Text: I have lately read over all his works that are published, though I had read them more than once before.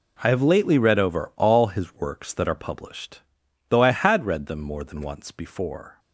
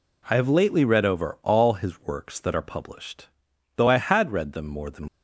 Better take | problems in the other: first | stops before "once before"; at 5.0 s

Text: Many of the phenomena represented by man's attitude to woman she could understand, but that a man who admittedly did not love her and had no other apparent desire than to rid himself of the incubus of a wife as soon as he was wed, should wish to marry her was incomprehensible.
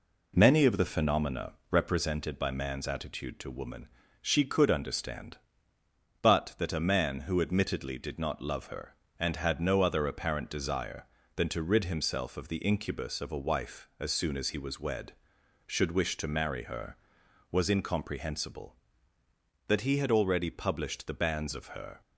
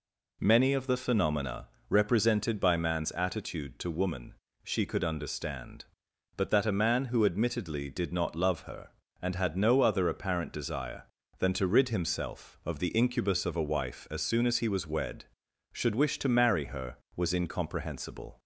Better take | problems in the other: second | pauses between "phenomena" and "represented"; slight; at 1.5 s; 0.18 s long; slight in the second // pauses between "woman" and "she"; slight; at 3.8 s; 0.34 s long; slight in the second // goes on to say "That he had already published the banns of her"; strong; from 19.6 s on; 2.3 s long

